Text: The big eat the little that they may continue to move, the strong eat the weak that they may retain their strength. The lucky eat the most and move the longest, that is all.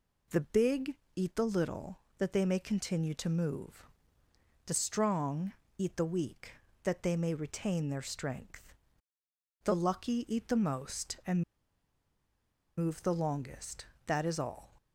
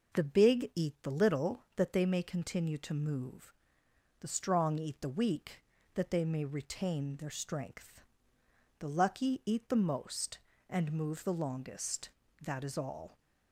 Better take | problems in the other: second | pauses between "big" and "eat"; slight; at 0.9 s; 0.20 s long // pauses between "strong" and "eat"; slight; at 5.5 s; 0.24 s long // pauses between "and" and "move"; strong; at 11.4 s; 1.3 s long

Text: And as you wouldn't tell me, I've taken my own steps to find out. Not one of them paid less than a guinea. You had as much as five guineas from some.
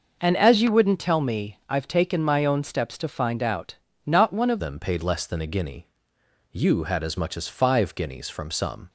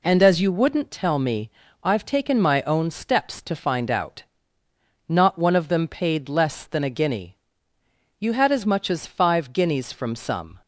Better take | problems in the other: second | changes voice at "them"; from 4.5 s on; 4.3 s long

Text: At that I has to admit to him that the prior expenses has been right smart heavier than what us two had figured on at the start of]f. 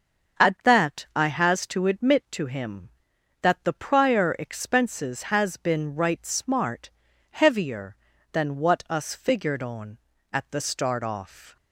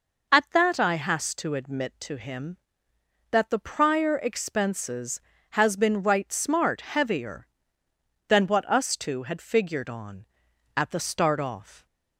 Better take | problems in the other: second | starts louder than the rest; until 1.5 s; 7 dB // pauses between "smart" and "heavier"; at 6.9 s; 0.40 s long // skips "two had"; at 9.1 s

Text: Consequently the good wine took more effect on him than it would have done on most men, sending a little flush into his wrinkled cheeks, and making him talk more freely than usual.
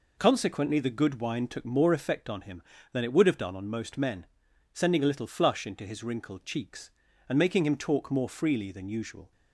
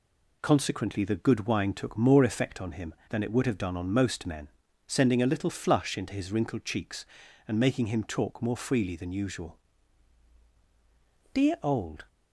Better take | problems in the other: first | goes on to say "Dear old"; noticeable; from 11.3 s on; 0.74 s long

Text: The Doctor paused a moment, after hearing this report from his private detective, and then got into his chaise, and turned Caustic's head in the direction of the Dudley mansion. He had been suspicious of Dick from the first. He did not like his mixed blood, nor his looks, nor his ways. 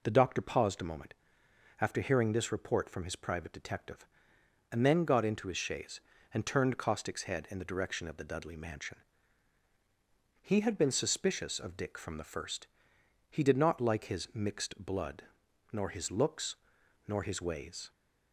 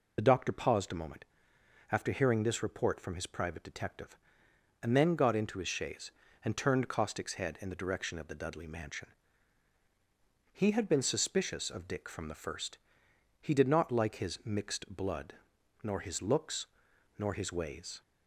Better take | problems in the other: first | loses the start of "The"; at 0.1 s; 25 ms

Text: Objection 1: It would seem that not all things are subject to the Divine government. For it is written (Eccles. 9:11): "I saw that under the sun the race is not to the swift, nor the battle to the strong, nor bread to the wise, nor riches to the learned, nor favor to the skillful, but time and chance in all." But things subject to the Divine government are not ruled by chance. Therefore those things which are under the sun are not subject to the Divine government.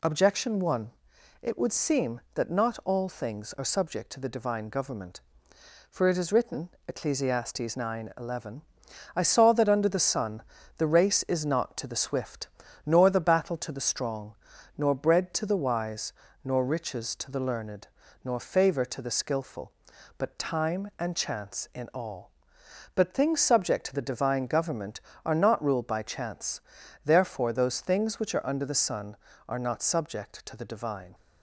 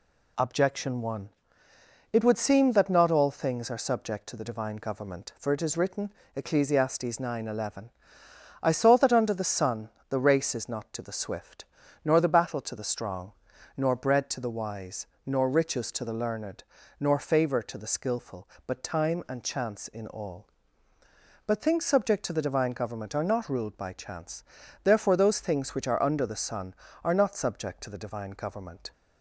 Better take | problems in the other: second | pauses between "sun" and "the"; slight; at 10.4 s; 0.34 s long; slight in the second // stops before "government"; at 31.1 s

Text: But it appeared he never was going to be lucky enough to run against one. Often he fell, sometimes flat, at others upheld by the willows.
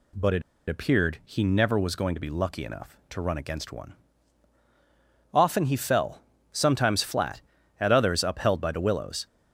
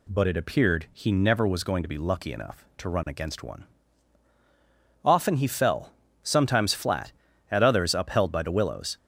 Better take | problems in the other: second | pauses between "it" and "appeared"; slight; at 0.4 s; 0.27 s long

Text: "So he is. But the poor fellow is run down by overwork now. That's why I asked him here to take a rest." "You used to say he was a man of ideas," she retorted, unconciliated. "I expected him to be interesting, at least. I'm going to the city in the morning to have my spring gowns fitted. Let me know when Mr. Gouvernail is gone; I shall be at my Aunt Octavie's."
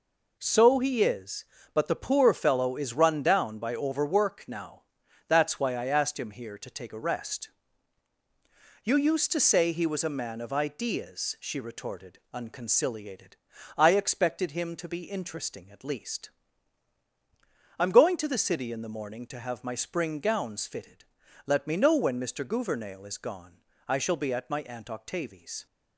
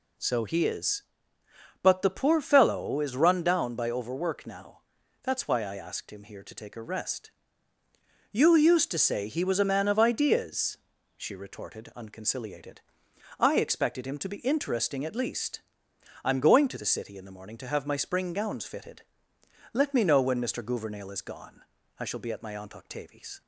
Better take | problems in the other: neither | none

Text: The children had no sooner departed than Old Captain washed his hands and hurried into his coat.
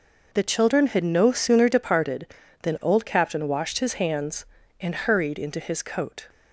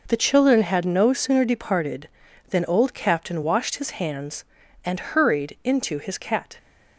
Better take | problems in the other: first | says "cat" for "coat"; at 6.1 s

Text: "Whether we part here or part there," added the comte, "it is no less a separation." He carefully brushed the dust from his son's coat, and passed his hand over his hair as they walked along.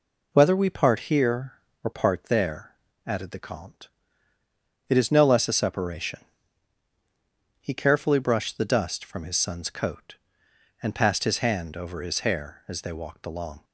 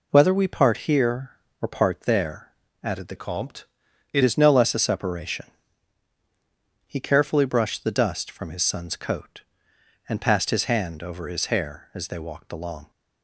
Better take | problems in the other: first | changes voice from "comte" to "it"; from 3.1 to 4.2 s; 1.1 s long

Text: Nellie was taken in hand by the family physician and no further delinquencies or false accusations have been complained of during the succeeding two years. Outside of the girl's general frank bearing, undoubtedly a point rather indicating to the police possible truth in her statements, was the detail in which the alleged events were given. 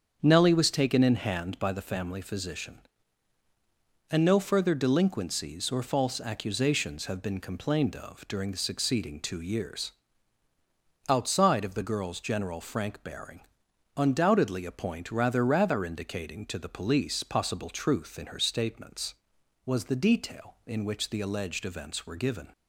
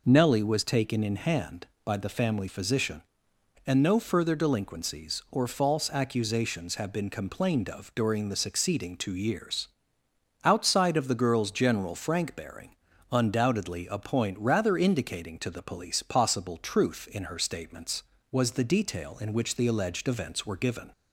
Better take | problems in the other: second | starts louder than the rest; strong; until 1.2 s; 7.5 dB // says "rather" twice; at 15.4 s

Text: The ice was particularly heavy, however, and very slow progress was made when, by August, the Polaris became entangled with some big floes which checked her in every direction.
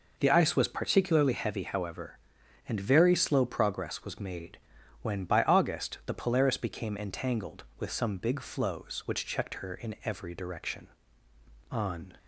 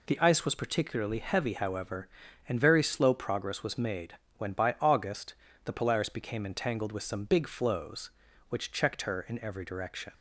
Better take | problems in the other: second | pauses between "made" and "when"; at 4.5 s; 0.45 s long; slight in the second // goes on to say "On"; slight; from 11.7 s on; 0.46 s long

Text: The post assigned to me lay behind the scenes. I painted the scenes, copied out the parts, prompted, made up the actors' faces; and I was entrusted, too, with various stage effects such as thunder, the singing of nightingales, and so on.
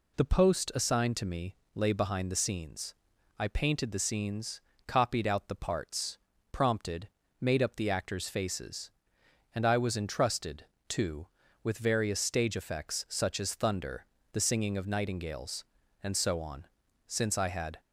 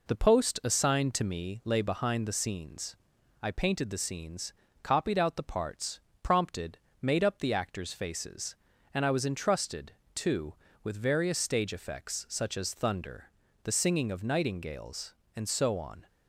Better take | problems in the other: second | pauses between "me" and "lay"; slight; at 1.5 s; 0.18 s long // goes on to say "Since I had"; noticeable; from 17.0 s on; 0.72 s long

